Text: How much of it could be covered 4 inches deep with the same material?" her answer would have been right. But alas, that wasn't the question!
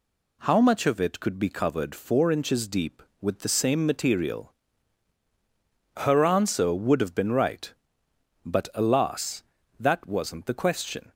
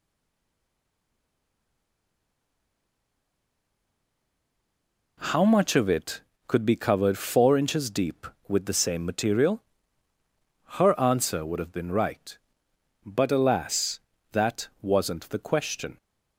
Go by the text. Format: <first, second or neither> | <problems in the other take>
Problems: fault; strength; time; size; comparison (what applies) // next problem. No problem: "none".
first | stays silent before the first word; strong; until 5.1 s; 5.1 s long // pauses between "that" and "wasn't"; slight; at 14.6 s; 0.15 s long